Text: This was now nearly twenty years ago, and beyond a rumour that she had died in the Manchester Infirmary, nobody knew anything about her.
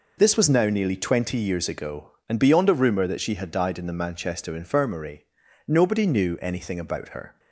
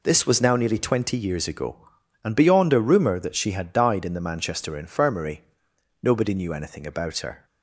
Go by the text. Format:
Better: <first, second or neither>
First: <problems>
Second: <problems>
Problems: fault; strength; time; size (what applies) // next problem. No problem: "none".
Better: neither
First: none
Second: none